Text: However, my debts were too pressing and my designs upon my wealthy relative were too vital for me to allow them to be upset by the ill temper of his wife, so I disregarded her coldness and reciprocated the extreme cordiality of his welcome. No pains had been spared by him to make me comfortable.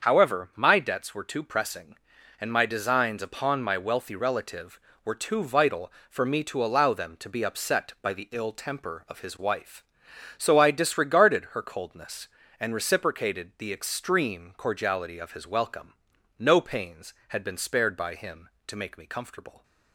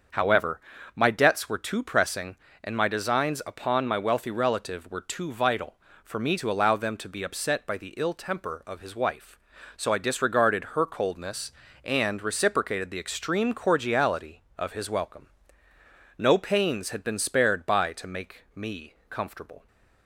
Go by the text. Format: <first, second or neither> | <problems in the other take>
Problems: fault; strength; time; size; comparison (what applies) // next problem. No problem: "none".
first | starts louder than the rest; until 1.4 s; 6.5 dB; also in the first // skips "him"; at 17.9 s // pauses between "me" and "comfortable"; slight; at 18.9 s; 0.16 s long